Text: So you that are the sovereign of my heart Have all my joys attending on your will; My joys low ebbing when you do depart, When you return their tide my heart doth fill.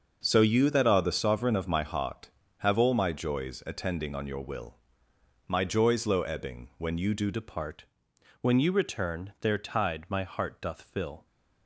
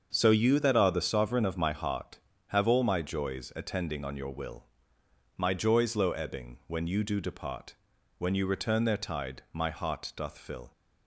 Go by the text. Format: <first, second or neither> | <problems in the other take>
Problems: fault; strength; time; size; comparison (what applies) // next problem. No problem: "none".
second | starts louder than the rest; until 1.2 s; 6 dB; also in the second // changes voice at "depart"; from 7.3 s on; 3.9 s long